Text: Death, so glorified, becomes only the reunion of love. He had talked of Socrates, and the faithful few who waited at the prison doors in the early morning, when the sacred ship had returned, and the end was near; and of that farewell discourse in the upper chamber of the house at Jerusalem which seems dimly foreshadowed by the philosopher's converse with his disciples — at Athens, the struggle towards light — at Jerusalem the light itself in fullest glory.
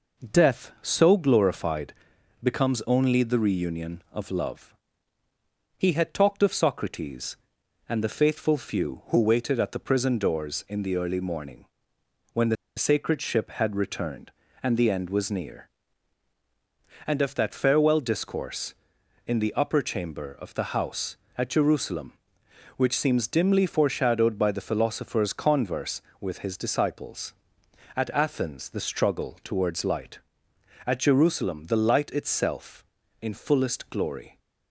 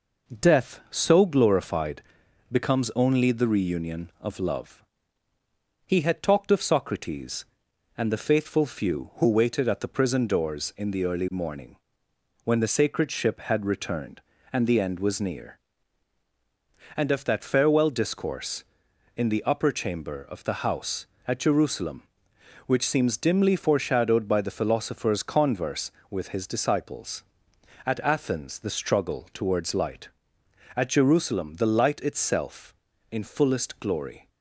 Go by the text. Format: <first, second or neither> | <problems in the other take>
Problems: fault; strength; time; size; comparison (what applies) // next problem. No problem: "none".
second | pauses between "the" and "sacred"; slight; at 12.5 s; 0.21 s long